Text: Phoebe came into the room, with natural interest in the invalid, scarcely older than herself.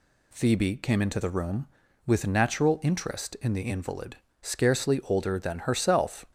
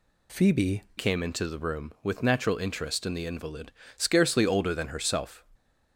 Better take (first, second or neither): first